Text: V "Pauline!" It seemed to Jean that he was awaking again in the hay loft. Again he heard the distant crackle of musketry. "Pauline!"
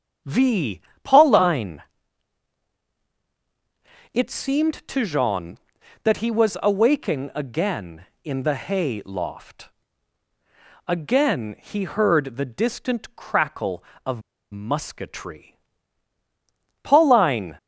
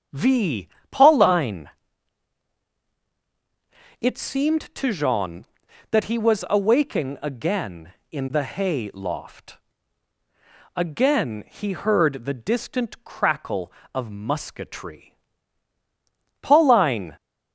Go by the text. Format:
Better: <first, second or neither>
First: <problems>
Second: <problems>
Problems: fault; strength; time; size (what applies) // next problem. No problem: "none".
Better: second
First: starts louder than the rest; strong; until 1.5 s; 8 dB // pauses between "V" and "Pauline"; slight; at 0.7 s; 0.24 s long // pauses between "of" and "musketry"; slight; at 14.2 s; 0.31 s long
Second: starts louder than the rest; strong; until 1.3 s; 8 dB // pauses between "V" and "Pauline"; slight; at 0.6 s; 0.24 s long